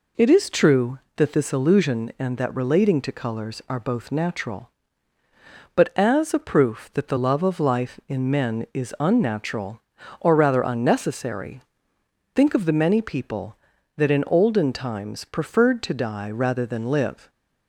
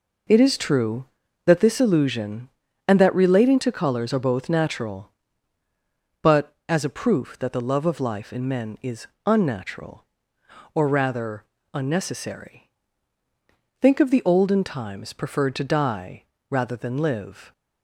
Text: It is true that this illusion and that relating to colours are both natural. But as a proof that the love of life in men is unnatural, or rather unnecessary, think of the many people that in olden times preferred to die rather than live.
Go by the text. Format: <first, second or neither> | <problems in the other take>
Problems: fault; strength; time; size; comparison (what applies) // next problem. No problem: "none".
first | pauses between "is" and "unnatural"; slight; at 9.0 s; 0.18 s long // pauses between "rather" and "unnecessary"; slight; at 11.4 s; 0.28 s long // skips "many people that in"; at 14.2 s // pauses between "die" and "rather"; slight; at 16.2 s; 0.26 s long